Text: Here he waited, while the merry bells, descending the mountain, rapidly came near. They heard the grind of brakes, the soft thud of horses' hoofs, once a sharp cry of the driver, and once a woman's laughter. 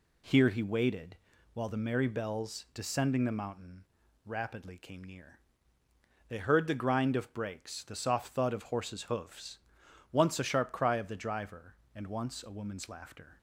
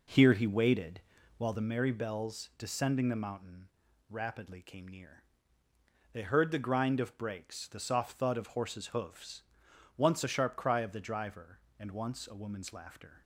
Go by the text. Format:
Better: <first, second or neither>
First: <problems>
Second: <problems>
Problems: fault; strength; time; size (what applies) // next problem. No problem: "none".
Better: first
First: none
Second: starts louder than the rest; noticeable; until 1.7 s; 4.5 dB